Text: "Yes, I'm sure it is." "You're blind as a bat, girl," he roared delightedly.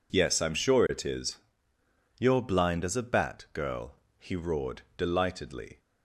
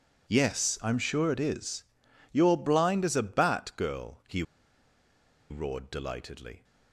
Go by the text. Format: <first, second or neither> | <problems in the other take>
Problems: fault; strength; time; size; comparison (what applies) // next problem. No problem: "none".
first | pauses between "he" and "roared"; at 4.4 s; 1.0 s long